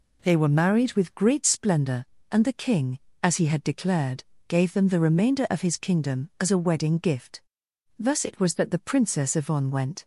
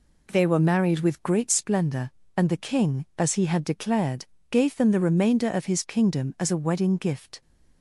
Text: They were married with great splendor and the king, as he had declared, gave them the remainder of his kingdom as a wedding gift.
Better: second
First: goes on to say "Thus it was that the Princess Yvonne went"; strong; from 7.9 s on; 2.0 s long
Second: none

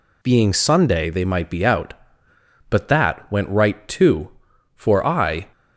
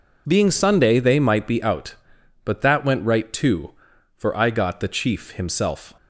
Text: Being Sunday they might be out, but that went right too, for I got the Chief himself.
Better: second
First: stops before "got the Chief himself"; at 5.5 s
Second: none

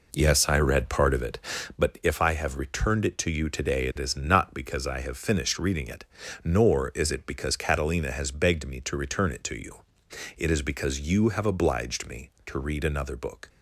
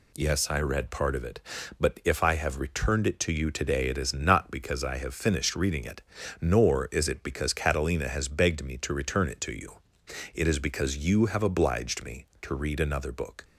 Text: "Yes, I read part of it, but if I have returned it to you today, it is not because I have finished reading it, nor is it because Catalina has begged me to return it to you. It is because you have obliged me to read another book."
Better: second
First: starts louder than the rest; noticeable; until 1.8 s; 4 dB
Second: none

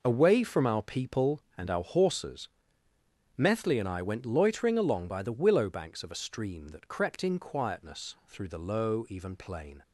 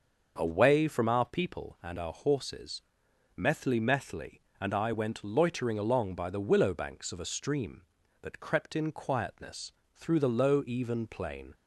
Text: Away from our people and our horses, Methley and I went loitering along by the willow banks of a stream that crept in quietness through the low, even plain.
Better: first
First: none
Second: starts louder than the rest; until 1.3 s; 6.5 dB // says "Methley" twice; at 3.7 s // pauses between "quietness" and "through"; slight; at 9.7 s; 0.24 s long

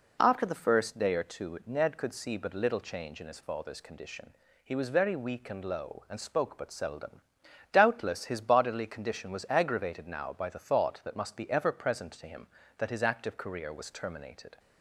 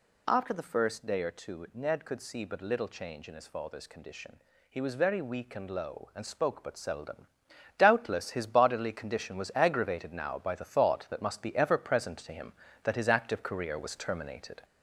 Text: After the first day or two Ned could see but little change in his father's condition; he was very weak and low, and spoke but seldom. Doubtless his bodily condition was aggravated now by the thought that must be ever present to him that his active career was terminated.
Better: first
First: none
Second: gets louder; noticeable; throughout; 4.5 dB

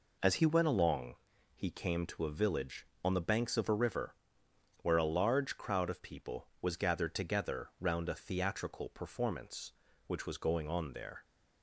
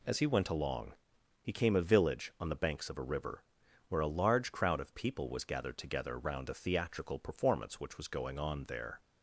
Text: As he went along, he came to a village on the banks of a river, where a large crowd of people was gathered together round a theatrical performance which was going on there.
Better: first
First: none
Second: skips "to"; at 1.7 s

